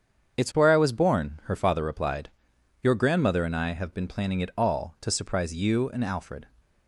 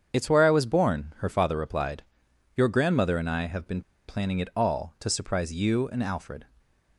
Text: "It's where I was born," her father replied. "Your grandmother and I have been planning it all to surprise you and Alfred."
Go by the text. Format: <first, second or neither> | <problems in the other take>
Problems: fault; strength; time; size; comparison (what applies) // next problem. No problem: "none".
first | starts louder than the rest; strong; until 1.2 s; 7.5 dB; strong in the first // pauses between "been" and "planning"; slight; at 3.8 s; 0.26 s long